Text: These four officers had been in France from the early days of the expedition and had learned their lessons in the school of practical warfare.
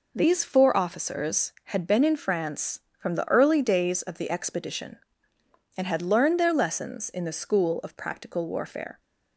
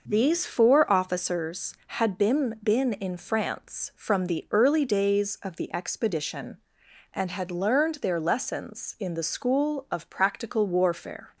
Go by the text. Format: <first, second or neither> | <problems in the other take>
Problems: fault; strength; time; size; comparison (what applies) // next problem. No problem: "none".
first | says "been" twice; at 2.6 s